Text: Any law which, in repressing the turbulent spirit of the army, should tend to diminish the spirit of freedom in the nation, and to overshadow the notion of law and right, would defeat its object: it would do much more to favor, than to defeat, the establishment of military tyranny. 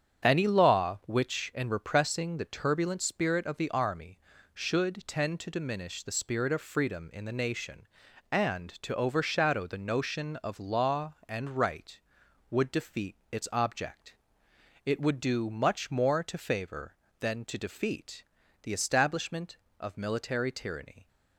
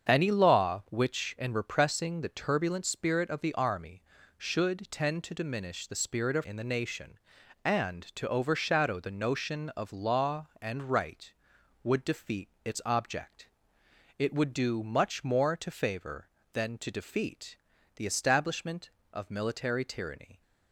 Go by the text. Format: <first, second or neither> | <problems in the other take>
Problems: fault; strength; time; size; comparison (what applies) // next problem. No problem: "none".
first | starts louder than the rest; strong; until 1.1 s; 7 dB; strong in the first // skips "freedom"; at 6.4 s // pauses between "defeat" and "its"; slight; at 12.4 s; 0.16 s long; slight in the first